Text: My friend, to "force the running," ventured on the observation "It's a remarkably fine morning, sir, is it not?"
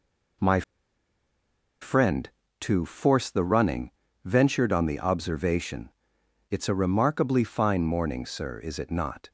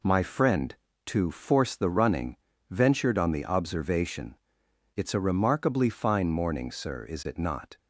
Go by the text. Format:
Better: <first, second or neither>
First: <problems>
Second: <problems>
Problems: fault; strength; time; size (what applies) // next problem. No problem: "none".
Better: second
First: pauses between "My" and "friend"; at 0.6 s; 1.1 s long // pauses between "observation" and "It's"; noticeable; at 5.8 s; 0.62 s long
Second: pauses between "observation" and "It's"; noticeable; at 4.3 s; 0.62 s long